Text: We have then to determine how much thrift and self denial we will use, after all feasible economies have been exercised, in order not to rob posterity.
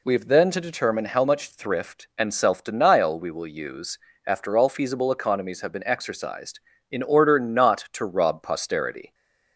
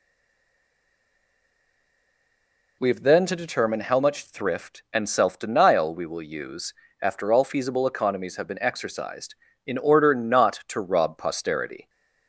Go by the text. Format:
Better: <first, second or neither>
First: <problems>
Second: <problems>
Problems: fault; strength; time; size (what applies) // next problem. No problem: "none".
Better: first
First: none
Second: stays silent before the first word; strong; until 2.7 s; 2.7 s long